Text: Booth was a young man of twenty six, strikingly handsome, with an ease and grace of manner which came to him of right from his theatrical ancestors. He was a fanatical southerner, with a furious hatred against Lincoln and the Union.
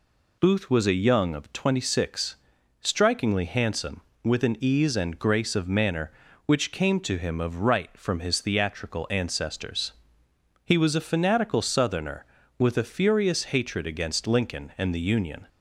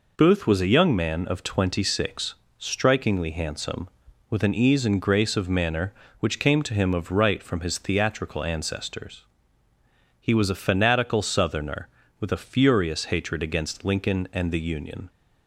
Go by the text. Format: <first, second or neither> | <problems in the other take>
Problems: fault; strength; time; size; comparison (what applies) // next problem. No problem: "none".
second | skips "man"; at 1.3 s